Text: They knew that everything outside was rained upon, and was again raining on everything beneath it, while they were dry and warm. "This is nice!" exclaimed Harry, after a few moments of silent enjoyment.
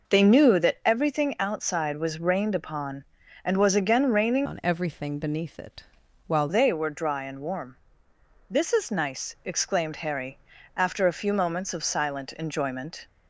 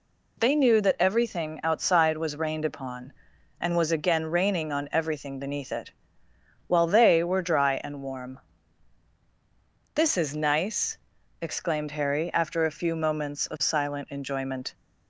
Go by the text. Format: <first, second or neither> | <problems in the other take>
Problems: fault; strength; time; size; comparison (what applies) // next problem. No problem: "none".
second | changes voice from "on" to "while"; from 4.4 to 6.4 s; 2.0 s long